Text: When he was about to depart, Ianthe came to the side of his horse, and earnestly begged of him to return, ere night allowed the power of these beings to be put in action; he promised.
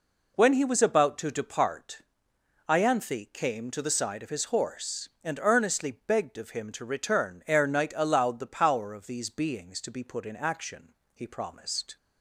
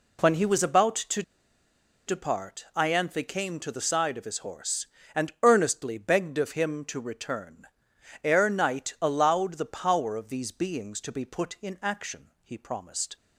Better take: first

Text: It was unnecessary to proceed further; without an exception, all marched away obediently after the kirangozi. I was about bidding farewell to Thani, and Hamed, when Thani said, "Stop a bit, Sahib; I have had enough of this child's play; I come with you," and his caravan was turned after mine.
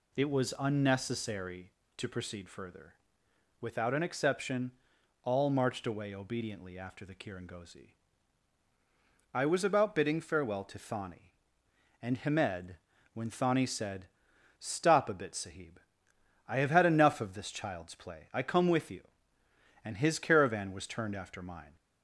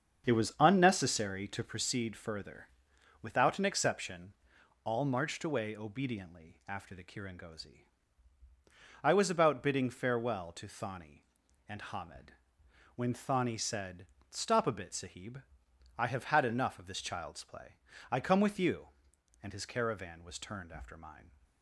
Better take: first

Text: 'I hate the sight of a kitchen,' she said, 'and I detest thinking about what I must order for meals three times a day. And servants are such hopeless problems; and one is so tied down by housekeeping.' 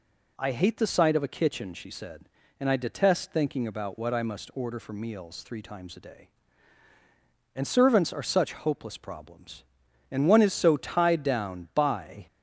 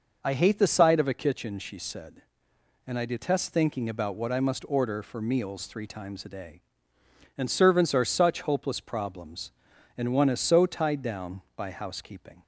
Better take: second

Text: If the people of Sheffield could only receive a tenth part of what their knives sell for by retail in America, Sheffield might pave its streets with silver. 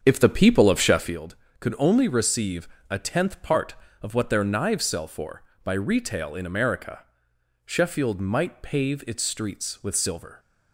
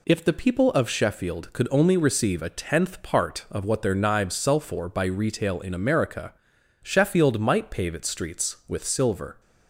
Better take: second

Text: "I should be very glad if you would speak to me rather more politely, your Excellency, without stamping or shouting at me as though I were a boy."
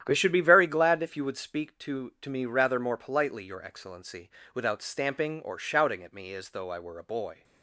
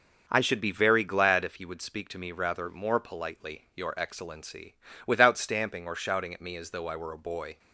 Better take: second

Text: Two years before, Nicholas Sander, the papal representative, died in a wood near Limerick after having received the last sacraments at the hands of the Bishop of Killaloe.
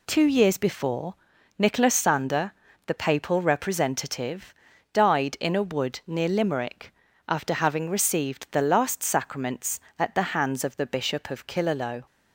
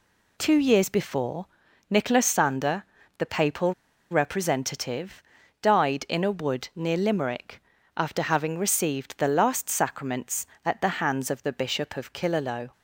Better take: first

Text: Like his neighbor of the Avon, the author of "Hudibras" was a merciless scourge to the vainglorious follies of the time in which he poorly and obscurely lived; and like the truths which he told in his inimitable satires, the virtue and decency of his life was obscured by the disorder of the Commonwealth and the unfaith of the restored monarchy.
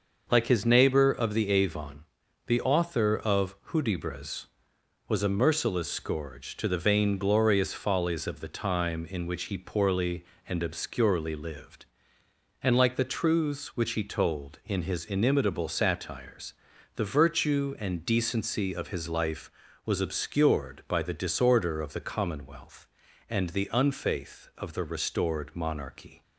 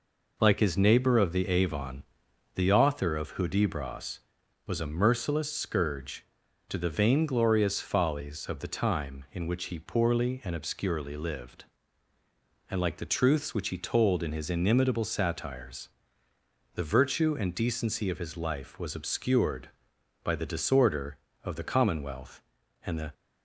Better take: first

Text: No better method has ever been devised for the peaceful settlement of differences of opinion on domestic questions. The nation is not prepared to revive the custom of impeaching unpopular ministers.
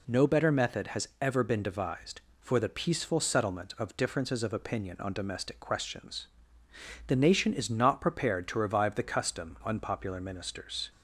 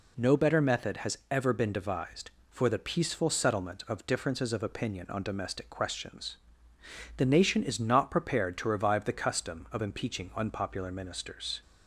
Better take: second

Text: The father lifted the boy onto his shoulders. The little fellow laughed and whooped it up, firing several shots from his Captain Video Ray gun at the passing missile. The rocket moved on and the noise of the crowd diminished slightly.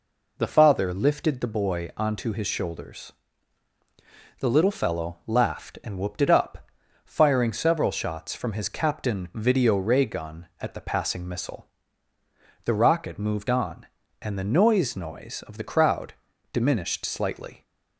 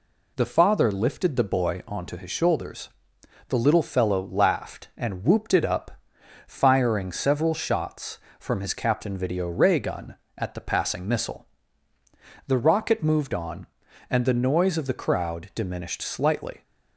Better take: second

